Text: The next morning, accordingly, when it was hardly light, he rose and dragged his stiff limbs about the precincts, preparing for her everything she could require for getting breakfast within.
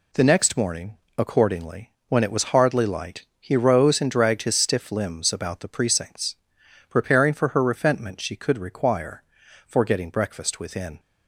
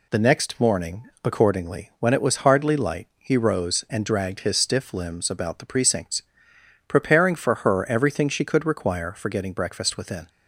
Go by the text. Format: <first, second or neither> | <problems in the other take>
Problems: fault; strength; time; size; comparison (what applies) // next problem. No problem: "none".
second | says "refentment" for "everything"; at 7.6 s